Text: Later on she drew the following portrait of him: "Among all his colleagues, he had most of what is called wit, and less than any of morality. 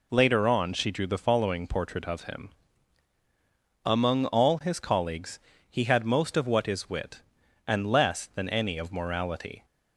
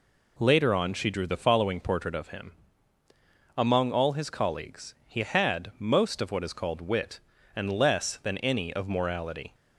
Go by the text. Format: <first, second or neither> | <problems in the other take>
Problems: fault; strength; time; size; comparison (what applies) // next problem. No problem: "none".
second | skips "called"; at 6.8 s